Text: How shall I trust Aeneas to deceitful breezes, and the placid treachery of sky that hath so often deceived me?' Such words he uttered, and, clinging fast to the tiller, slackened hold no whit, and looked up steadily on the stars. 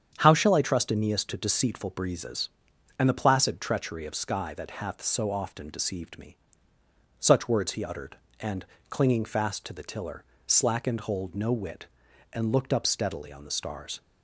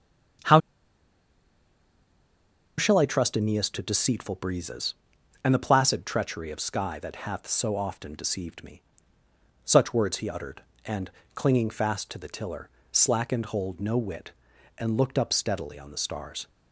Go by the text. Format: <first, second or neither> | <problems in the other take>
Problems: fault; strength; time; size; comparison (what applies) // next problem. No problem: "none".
first | starts louder than the rest; strong; until 3.6 s; 8 dB; strong in the first // pauses between "How" and "shall"; strong; at 0.5 s; 2.1 s long